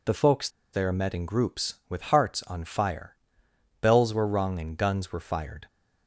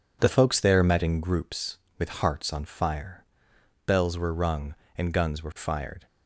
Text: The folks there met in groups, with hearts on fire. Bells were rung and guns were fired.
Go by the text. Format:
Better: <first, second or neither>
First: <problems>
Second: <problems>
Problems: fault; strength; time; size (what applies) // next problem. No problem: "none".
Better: second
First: pauses between "folks" and "there"; slight; at 0.4 s; 0.24 s long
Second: none